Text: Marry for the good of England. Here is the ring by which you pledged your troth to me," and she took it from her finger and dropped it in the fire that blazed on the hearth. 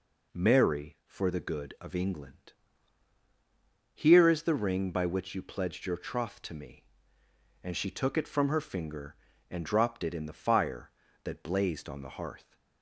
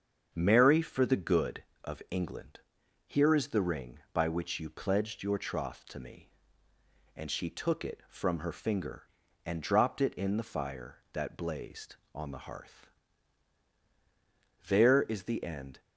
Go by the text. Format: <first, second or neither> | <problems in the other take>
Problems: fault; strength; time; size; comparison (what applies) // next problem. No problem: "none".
first | starts louder than the rest; until 1.3 s; 7 dB // goes on to say "There is the end"; noticeable; from 14.6 s on; 1.1 s long